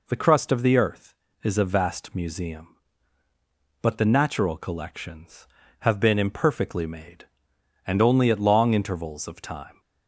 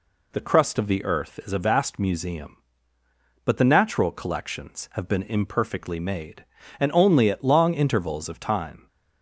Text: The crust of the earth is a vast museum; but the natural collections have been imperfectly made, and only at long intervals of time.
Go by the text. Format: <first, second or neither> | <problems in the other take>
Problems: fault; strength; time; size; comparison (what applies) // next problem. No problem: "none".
neither | none